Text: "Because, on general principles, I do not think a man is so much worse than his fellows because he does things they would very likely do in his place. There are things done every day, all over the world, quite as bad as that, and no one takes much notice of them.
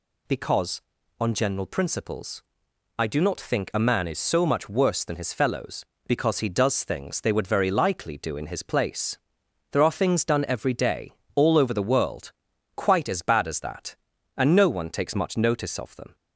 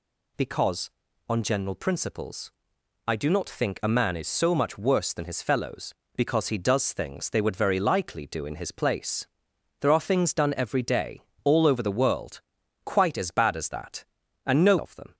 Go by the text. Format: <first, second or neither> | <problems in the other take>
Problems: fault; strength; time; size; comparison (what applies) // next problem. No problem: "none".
first | skips "one takes much notice"; at 14.7 s